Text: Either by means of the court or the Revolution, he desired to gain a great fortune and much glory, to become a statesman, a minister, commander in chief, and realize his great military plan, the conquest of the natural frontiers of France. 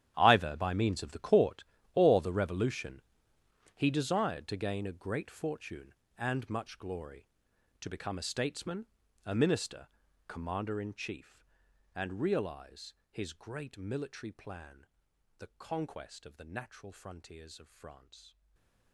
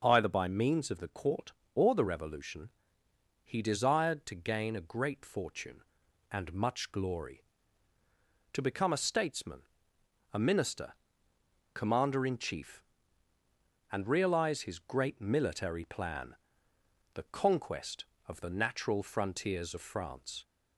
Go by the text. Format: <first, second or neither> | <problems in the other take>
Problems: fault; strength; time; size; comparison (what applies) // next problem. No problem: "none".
second | gets quieter; strong; throughout; 16 dB // pauses between "realize" and "his"; slight; at 12.9 s; 0.16 s long // stays silent after the last word; slight; from 18.2 s on; 0.7 s long